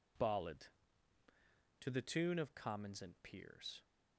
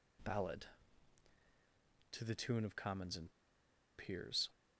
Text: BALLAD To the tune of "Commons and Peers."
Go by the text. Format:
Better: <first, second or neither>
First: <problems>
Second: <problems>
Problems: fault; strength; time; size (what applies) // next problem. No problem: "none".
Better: first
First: none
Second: pauses between "and" and "Peers"; noticeable; at 3.3 s; 0.68 s long